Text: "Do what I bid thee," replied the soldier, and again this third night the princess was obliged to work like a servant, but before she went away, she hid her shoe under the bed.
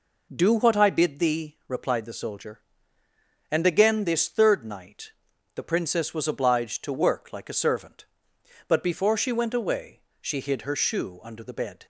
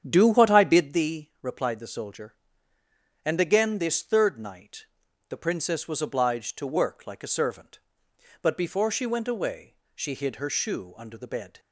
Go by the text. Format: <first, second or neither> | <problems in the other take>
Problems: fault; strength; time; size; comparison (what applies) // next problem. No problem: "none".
first | starts louder than the rest; strong; until 1.0 s; 8.5 dB // pauses between "night" and "the"; at 4.8 s; 0.44 s long; also in the first